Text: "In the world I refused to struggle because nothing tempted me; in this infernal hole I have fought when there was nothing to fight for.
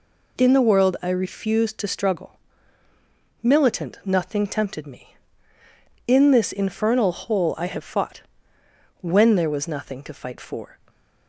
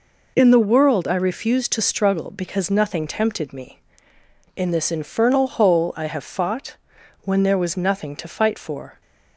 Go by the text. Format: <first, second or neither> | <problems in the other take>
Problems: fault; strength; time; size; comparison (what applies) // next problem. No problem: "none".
second | says "militant" for "because"; at 3.4 s // pauses between "fought" and "when"; noticeable; at 8.2 s; 0.80 s long; noticeable in the second